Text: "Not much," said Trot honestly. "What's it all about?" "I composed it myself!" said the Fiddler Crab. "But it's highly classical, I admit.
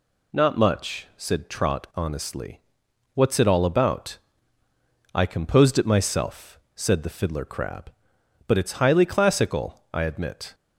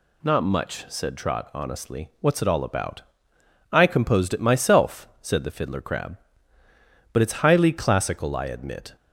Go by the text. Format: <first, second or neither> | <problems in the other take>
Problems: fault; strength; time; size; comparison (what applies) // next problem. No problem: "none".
neither | none